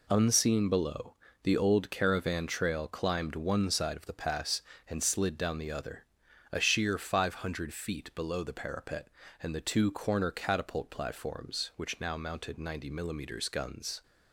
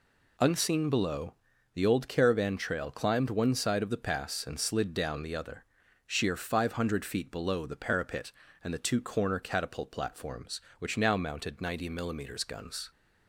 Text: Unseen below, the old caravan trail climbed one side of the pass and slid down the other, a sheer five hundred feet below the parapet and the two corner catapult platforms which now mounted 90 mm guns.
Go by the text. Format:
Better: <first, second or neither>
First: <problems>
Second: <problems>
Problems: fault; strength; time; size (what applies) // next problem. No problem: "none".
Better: first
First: none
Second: skips "a"; at 5.8 s